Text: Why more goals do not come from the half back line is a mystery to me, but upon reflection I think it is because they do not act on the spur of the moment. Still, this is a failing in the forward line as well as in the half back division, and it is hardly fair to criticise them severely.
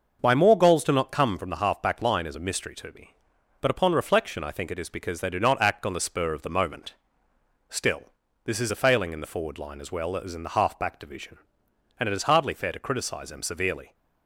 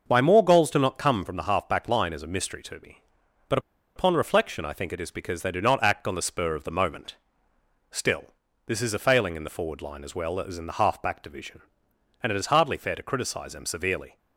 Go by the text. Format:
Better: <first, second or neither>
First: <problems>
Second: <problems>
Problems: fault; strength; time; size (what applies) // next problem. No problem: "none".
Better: first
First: starts louder than the rest; noticeable; until 1.2 s; 6 dB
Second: starts louder than the rest; noticeable; until 1.0 s; 6 dB // pauses between "but" and "upon"; at 3.5 s; 0.37 s long